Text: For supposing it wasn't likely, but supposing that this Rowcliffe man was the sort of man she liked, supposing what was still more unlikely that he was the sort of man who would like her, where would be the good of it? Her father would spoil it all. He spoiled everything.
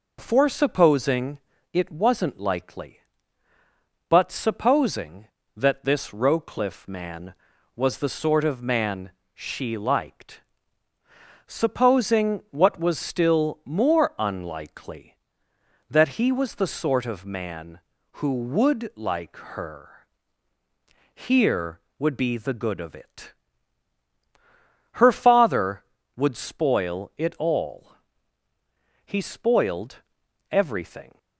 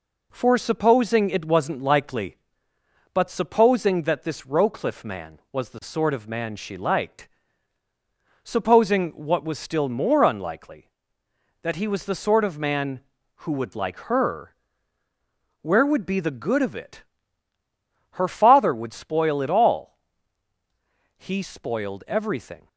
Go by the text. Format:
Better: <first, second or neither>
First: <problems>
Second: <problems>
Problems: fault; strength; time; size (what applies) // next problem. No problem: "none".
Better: second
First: pauses between "supposing" and "it"; slight; at 1.3 s; 0.32 s long // pauses between "man" and "she"; slight; at 9.1 s; 0.22 s long // pauses between "like" and "her"; slight; at 19.3 s; 0.18 s long // says "here" for "where"; at 21.1 s // pauses between "spoiled" and "everything"; noticeable; at 29.9 s; 0.52 s long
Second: none